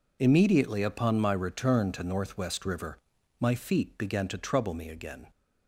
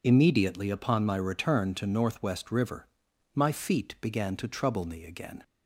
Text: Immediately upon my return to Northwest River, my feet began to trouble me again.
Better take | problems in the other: neither | none

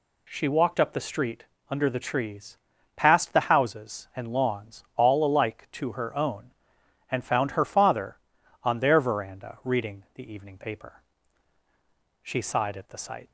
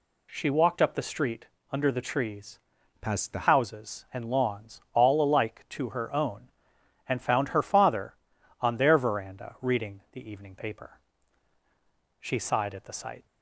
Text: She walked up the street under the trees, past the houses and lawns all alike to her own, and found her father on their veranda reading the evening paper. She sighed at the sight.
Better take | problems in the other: first | pauses between "street" and "under"; slight; at 1.4 s; 0.24 s long; slight in the first // changes voice from "past" to "the"; from 3.0 to 3.4 s; 0.4 s long

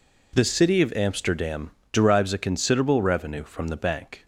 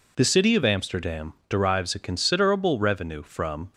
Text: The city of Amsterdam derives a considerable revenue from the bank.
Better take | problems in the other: first | pauses between "Amsterdam" and "derives"; slight; at 1.3 s; 0.16 s long; slight in the first // stops before "the bank"; at 3.7 s

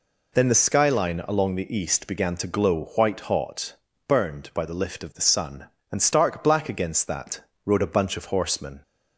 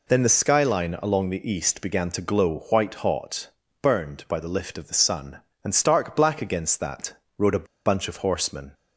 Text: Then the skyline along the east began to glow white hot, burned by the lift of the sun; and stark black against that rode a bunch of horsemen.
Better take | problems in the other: first | pauses between "that" and "rode"; slight; at 7.1 s; 0.26 s long; slight in the first // pauses between "a" and "bunch"; slight; at 7.6 s; 0.21 s long

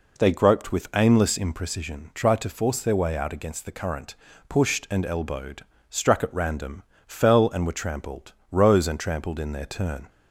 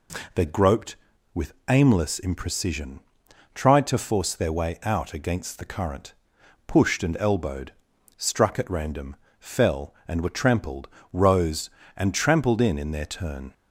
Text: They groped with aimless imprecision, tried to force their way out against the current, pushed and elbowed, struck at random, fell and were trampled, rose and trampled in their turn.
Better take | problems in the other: first | pauses between "with" and "aimless"; slight; at 1.5 s; 0.16 s long // says "in" twice; at 12.7 s

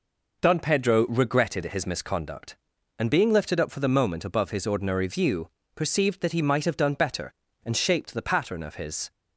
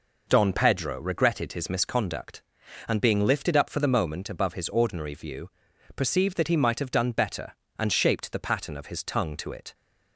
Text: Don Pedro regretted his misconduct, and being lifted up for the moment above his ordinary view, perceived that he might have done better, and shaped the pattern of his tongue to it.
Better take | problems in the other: second | stops before "tongue to it"; at 9.1 s

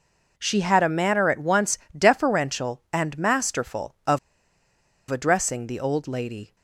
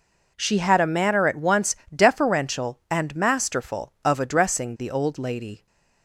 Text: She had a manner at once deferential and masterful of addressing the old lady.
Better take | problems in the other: second | pauses between "once" and "deferential"; slight; at 1.7 s; 0.20 s long; slight in the second // pauses between "of" and "addressing"; noticeable; at 4.1 s; 0.92 s long

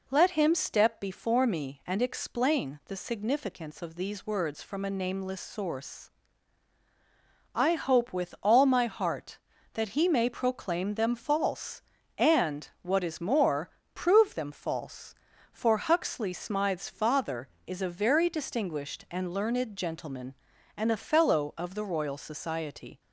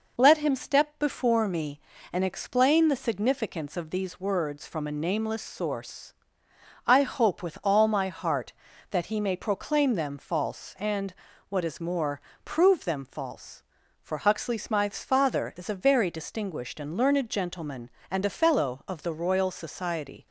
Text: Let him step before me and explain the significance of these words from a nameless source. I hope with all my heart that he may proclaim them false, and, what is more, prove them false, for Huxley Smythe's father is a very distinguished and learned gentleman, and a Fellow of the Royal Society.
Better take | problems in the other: neither | none

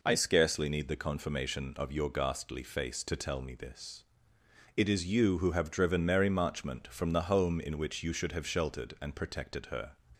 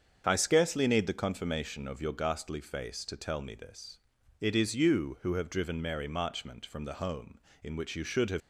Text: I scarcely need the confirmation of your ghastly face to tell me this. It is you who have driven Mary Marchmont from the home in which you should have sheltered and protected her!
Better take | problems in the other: first | starts louder than the rest; until 1.2 s; 7 dB // stops before "sheltered and protected her"; at 8.4 s

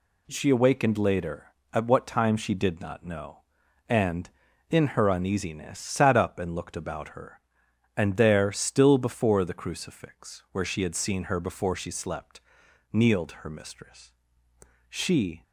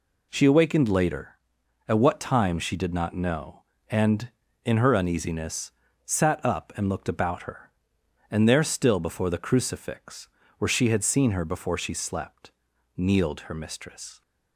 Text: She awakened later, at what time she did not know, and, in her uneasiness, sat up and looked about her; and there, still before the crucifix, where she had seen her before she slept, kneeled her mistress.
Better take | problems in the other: second | goes on to say "She"; from 14.8 s on; 0.54 s long

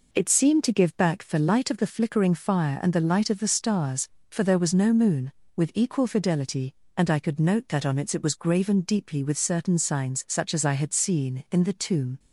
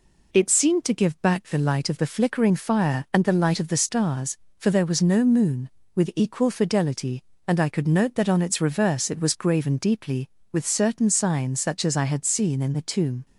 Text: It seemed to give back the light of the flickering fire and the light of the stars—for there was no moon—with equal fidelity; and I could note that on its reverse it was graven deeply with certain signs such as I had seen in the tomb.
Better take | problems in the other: second | skips "reverse"; at 8.1 s

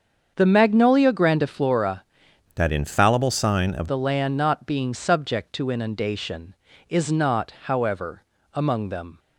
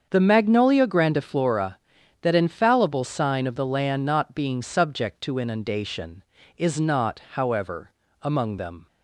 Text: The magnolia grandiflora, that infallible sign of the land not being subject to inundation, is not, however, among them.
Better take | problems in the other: second | starts louder than the rest; until 1.3 s; 7 dB; also in the second // changes voice from "that" to "of"; from 2.5 to 3.8 s; 1.3 s long

